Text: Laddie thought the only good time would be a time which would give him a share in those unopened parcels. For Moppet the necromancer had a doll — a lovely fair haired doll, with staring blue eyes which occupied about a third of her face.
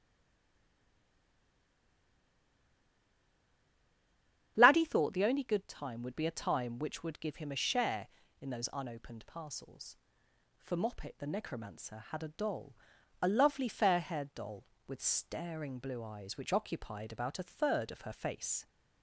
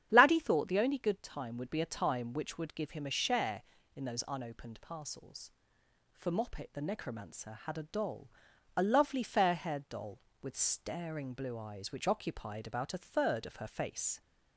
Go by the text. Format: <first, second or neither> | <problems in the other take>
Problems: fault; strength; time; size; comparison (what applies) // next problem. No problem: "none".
second | stays silent before the first word; strong; until 4.5 s; 4.5 s long // starts louder than the rest; strong; until 5.5 s; 9 dB; strong in the second